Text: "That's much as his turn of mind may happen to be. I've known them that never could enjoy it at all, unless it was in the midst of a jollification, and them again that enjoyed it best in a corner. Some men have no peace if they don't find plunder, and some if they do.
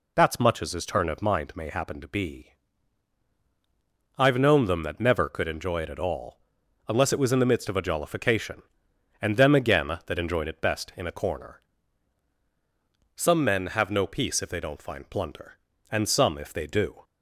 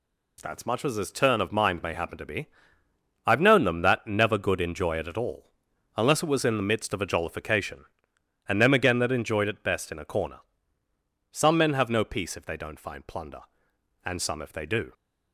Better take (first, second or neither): first